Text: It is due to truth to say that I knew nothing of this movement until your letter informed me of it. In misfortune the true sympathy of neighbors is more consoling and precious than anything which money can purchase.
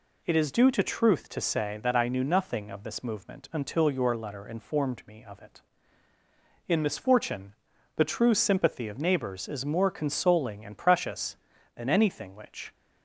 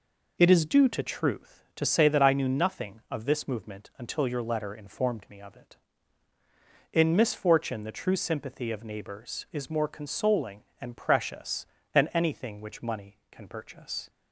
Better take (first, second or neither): second